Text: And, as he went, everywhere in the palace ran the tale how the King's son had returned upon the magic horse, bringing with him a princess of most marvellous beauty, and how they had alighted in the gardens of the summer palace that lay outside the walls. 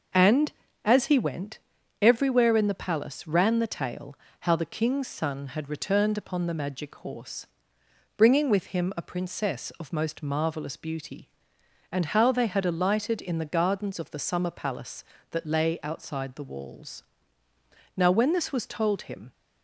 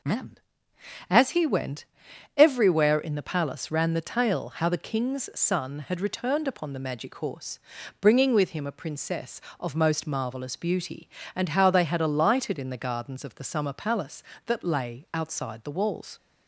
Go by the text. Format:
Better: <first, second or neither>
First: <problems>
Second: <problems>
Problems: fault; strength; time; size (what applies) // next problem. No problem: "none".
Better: second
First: starts louder than the rest; noticeable; until 1.4 s; 6 dB // pauses between "tale" and "how"; slight; at 4.1 s; 0.26 s long // goes on to say "Now when this was told him"; from 17.9 s on; 1.3 s long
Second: none